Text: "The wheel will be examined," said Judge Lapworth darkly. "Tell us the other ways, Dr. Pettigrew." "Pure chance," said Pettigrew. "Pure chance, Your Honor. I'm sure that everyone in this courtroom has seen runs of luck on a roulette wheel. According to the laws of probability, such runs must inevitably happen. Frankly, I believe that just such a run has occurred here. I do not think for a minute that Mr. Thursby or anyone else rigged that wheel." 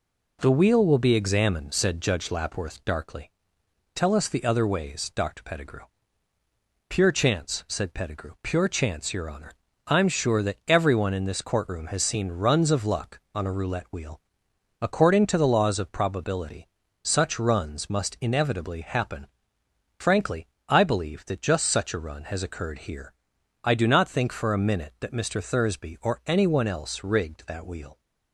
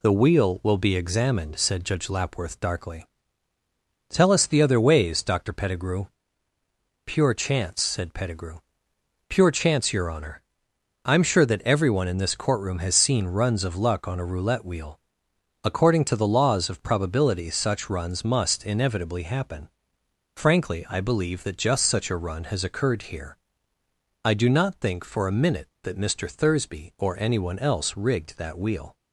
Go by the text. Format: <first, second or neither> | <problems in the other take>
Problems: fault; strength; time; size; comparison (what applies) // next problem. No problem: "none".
neither | none